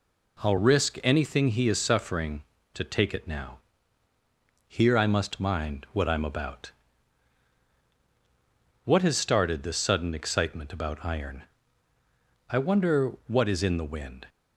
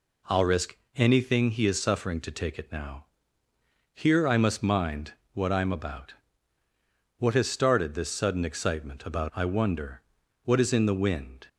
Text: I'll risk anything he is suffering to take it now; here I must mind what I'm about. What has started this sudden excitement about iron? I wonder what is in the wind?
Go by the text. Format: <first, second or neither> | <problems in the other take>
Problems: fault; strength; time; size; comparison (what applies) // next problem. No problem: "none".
first | pauses between "risk" and "anything"; slight; at 0.7 s; 0.20 s long // pauses between "mind" and "what"; slight; at 5.1 s; 0.22 s long // skips "iron"; at 9.3 s // pauses between "wonder" and "what"; at 10.0 s; 0.42 s long